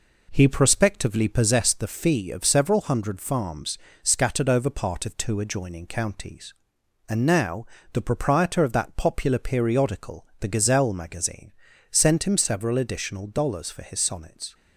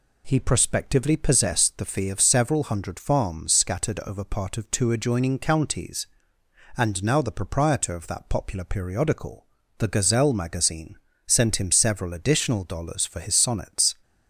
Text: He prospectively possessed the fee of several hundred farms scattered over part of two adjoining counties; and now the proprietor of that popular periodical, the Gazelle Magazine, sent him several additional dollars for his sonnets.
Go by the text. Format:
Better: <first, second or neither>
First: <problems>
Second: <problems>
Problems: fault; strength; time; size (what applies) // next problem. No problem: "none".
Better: second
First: starts louder than the rest; noticeable; until 1.7 s; 4 dB // pauses between "farms" and "scattered"; slight; at 3.7 s; 0.24 s long // pauses between "now" and "the"; slight; at 7.6 s; 0.28 s long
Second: none